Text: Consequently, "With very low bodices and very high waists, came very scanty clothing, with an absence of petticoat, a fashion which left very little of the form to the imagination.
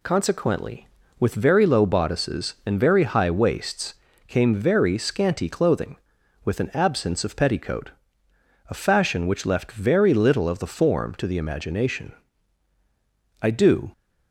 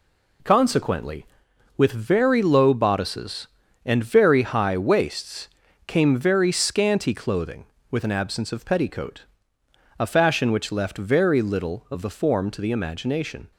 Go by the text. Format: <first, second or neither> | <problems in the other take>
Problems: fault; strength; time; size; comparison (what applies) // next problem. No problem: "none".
second | goes on to say "I do"; from 13.4 s on; 0.52 s long